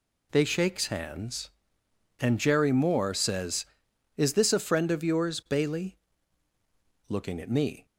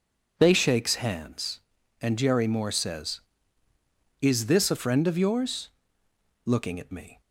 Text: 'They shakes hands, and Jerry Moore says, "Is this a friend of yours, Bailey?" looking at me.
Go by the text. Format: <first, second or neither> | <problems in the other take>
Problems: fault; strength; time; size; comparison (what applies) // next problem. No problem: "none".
first | skips "Bailey"; at 6.0 s